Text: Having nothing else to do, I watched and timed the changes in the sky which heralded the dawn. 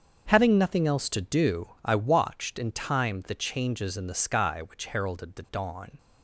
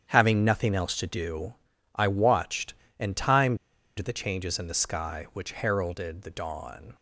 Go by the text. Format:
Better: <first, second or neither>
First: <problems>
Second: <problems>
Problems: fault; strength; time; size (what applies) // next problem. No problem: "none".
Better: first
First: starts louder than the rest; until 1.2 s; 7 dB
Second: starts louder than the rest; strong; until 1.1 s; 8.5 dB // pauses between "timed" and "the"; at 3.5 s; 0.42 s long